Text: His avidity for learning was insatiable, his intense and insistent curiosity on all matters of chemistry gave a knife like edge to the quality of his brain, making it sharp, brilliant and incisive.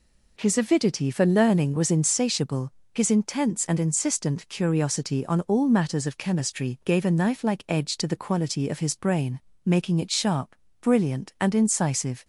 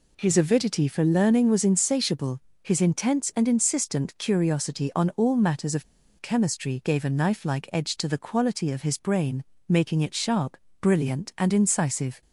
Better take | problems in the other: first | pauses between "of" and "chemistry"; at 5.8 s; 0.37 s long

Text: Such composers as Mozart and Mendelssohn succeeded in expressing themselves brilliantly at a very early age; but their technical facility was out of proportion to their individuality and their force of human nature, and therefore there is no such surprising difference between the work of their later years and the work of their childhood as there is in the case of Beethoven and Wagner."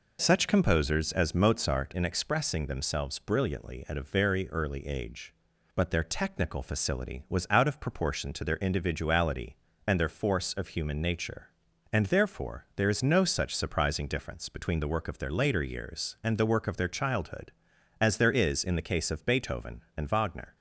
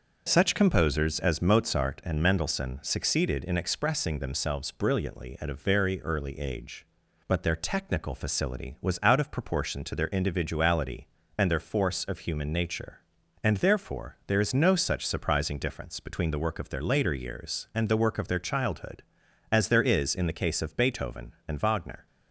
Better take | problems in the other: second | skips "and Mendelssohn succeeded"; at 1.9 s

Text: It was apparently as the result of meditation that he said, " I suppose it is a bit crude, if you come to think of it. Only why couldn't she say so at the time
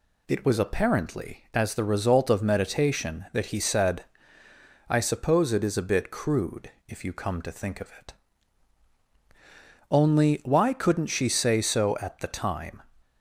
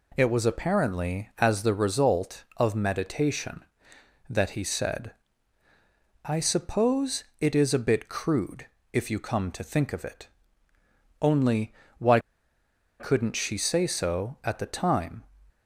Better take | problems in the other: first | pauses between "suppose" and "it"; slight; at 7.2 s; 0.18 s long // pauses between "Only" and "why"; slight; at 11.7 s; 0.24 s long // pauses between "why" and "couldn't"; noticeable; at 12.1 s; 0.81 s long

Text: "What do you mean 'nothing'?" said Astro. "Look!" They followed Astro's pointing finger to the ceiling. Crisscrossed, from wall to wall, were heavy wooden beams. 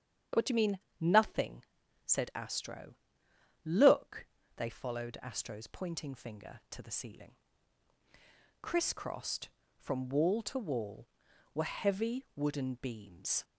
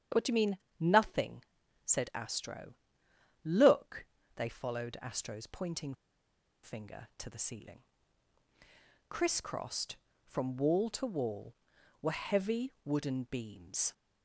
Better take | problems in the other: first | starts louder than the rest; strong; until 1.3 s; 8.5 dB; strong in the first // pauses between "mean" and "nothing"; slight; at 0.5 s; 0.20 s long; slight in the first // pauses between "pointing" and "finger"; noticeable; at 5.9 s; 0.68 s long

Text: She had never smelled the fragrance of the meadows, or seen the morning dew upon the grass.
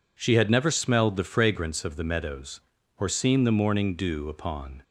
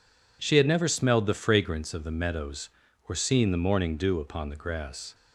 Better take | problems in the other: second | stops before "the grass"; at 4.8 s

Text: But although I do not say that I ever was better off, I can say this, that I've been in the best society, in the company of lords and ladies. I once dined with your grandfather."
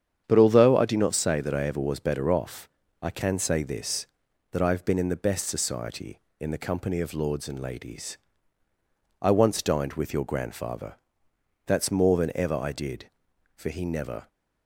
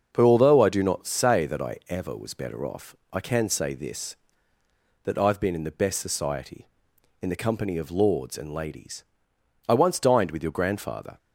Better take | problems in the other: second | starts louder than the rest; strong; until 1.2 s; 8.5 dB; also in the second // goes on to say "That's more than ever I did for he never"; strong; from 11.6 s on; 2.6 s long

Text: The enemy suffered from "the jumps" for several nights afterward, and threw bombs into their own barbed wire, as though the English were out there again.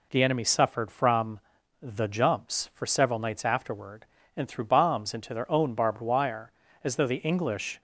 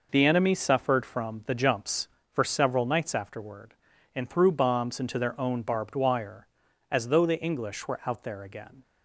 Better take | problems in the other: second | pauses between "from" and "the"; at 1.4 s; 0.42 s long // stops before "were out there again"; at 7.7 s

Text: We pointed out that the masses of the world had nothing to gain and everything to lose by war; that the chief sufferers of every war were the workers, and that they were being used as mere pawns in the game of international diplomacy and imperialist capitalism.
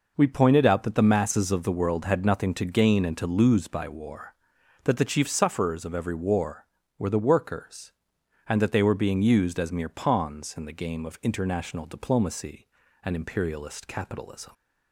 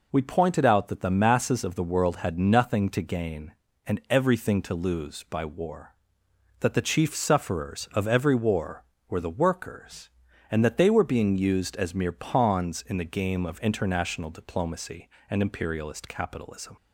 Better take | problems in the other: second | skips "everything"; at 3.1 s

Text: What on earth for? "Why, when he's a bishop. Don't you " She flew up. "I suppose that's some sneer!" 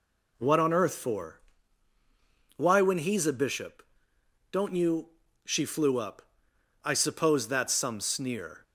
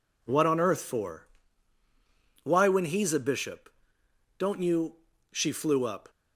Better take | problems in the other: first | stops before "I suppose that's some sneer"; at 6.0 s

